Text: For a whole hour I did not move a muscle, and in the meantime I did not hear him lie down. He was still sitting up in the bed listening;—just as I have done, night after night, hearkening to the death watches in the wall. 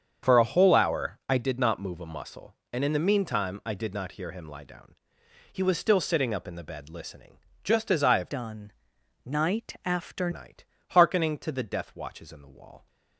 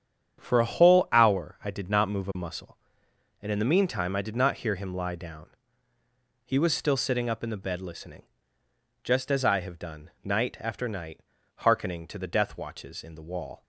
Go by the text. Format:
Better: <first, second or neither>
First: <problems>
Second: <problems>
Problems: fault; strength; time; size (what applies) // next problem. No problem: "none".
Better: second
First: starts louder than the rest; strong; until 1.3 s; 7.5 dB // changes voice from "done" to "after"; from 8.3 to 10.2 s; 1.9 s long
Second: starts louder than the rest; strong; until 1.4 s; 8.5 dB